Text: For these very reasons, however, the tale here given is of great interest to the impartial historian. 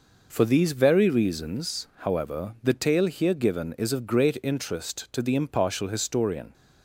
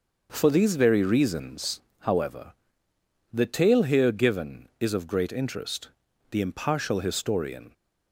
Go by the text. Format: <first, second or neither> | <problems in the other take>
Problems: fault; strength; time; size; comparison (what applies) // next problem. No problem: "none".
first | starts louder than the rest; noticeable; until 1.3 s; 6 dB // skips "to"; at 6.0 s